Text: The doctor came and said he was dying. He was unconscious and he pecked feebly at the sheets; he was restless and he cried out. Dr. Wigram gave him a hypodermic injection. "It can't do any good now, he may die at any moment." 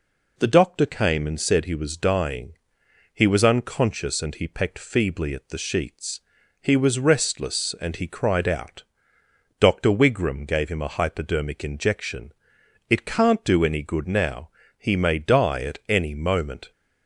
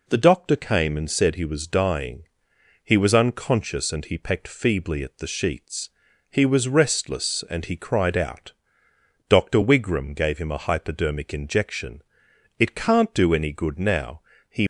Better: first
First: none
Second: stops before "may die at any moment"; at 14.6 s

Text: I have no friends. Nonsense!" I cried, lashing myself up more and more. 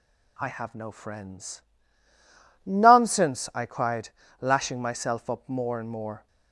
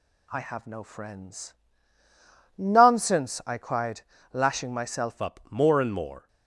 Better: first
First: none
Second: changes voice at "up"; from 5.1 s on; 1.1 s long

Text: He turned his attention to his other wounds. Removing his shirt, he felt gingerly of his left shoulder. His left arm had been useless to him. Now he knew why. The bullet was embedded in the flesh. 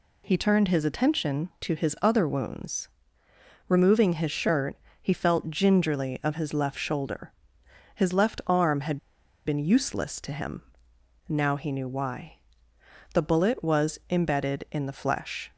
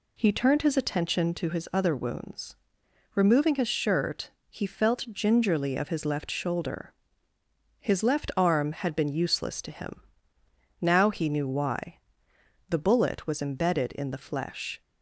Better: second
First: pauses between "had" and "been"; noticeable; at 8.9 s; 0.48 s long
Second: none

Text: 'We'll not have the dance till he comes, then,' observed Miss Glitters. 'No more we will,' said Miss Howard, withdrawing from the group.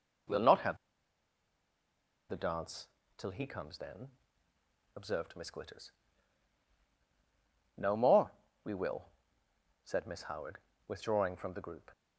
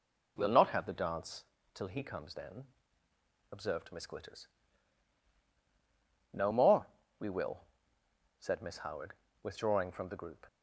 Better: second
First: pauses between "have" and "the"; strong; at 0.7 s; 1.5 s long // pauses between "dance" and "till"; slight; at 2.8 s; 0.28 s long // pauses between "more" and "we"; slight; at 8.3 s; 0.32 s long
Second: pauses between "dance" and "till"; slight; at 1.4 s; 0.28 s long // pauses between "more" and "we"; slight; at 6.8 s; 0.32 s long

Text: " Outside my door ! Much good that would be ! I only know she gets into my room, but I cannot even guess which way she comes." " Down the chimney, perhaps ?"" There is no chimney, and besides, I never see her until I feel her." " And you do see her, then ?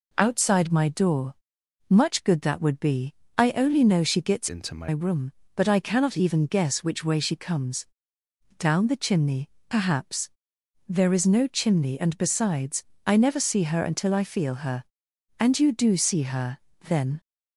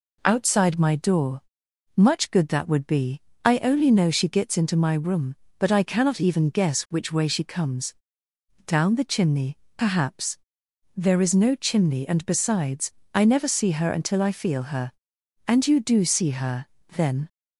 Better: second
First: changes voice from "into" to "my"; from 4.4 to 4.8 s; 0.4 s long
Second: none

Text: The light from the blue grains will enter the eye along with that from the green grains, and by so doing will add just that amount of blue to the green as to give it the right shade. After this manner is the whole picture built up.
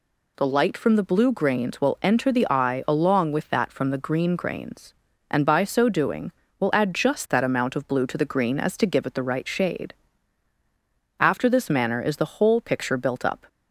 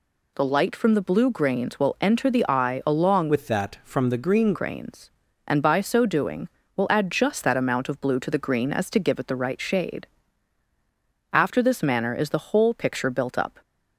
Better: first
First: none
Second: changes voice from "with" to "green"; from 3.2 to 4.5 s; 1.3 s long

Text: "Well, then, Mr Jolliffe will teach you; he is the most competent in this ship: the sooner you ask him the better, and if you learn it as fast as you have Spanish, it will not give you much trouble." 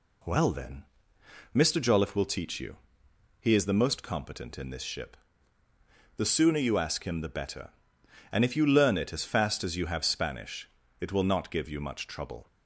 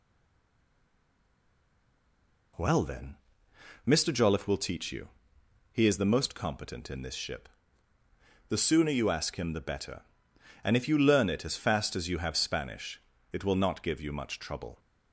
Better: first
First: none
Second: stays silent before the first word; strong; until 2.5 s; 2.5 s long

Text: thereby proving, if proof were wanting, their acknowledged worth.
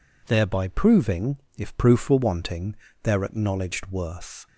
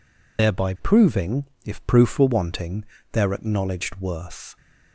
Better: first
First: none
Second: loses the start of "thereby"; at 0.3 s; 100 ms

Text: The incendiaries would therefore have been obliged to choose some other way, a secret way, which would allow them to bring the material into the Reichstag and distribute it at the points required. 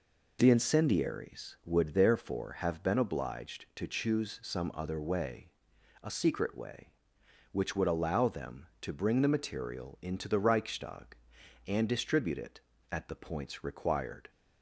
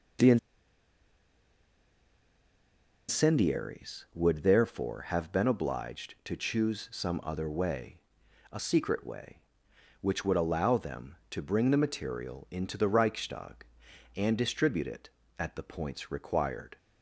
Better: first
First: none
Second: pauses between "The" and "incendiaries"; strong; at 0.3 s; 2.7 s long

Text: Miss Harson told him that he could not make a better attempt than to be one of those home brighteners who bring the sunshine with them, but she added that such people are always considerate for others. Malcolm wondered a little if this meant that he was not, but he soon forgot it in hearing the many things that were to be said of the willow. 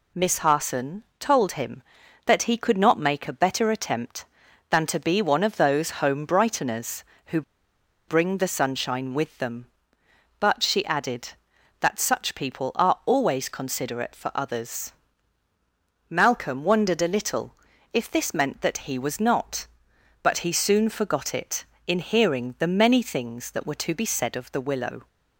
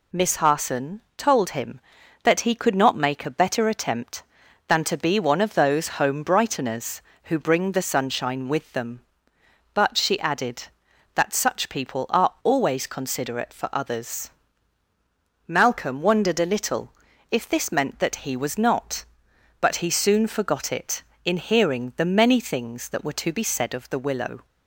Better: second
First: pauses between "Harson" and "told"; slight; at 1.0 s; 0.16 s long // pauses between "who" and "bring"; noticeable; at 7.4 s; 0.66 s long // pauses between "little" and "if"; at 17.5 s; 0.38 s long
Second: pauses between "Harson" and "told"; slight; at 0.9 s; 0.16 s long // pauses between "little" and "if"; at 16.9 s; 0.38 s long

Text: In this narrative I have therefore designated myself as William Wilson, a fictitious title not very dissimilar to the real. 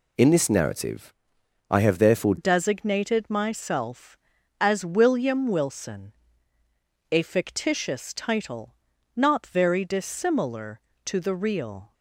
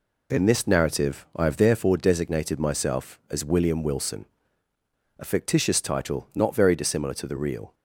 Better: second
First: pauses between "narrative" and "I"; noticeable; at 1.1 s; 0.58 s long // changes voice at "designated"; from 2.3 s on; 9.6 s long // pauses between "title" and "not"; at 8.7 s; 0.40 s long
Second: none

